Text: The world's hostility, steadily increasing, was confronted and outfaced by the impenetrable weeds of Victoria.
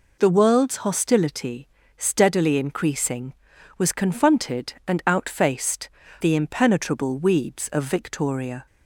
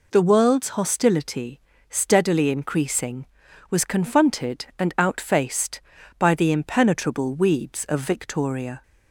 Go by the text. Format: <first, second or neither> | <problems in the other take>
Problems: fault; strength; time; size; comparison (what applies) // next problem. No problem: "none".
second | skips "by"; at 6.0 s